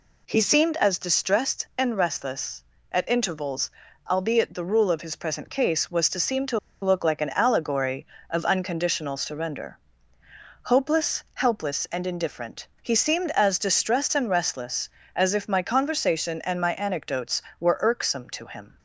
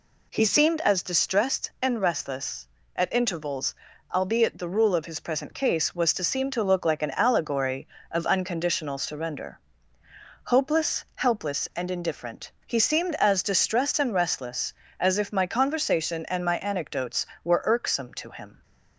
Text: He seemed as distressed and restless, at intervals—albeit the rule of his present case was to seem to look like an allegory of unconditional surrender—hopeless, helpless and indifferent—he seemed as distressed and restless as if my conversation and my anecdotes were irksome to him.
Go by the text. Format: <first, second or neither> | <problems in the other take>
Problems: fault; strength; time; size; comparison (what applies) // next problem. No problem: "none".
second | pauses between "to" and "look"; slight; at 6.5 s; 0.24 s long